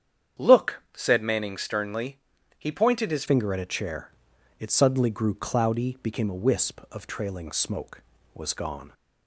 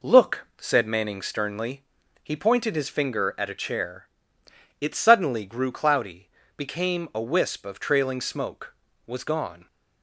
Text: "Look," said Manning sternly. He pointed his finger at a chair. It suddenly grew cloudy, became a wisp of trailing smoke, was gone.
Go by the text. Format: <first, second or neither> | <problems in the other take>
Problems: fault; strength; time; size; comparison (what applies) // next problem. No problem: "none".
second | starts louder than the rest; strong; until 1.5 s; 8.5 dB // changes voice at "finger"; from 3.2 s on; 5.7 s long